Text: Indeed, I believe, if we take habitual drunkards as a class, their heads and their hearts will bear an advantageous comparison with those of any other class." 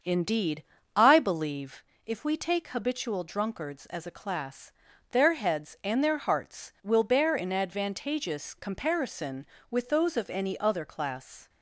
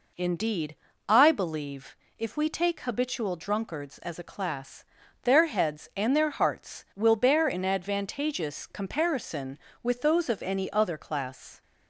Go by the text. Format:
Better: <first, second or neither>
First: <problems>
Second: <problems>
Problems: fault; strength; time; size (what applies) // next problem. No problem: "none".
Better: second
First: starts louder than the rest; until 1.8 s; 6.5 dB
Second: none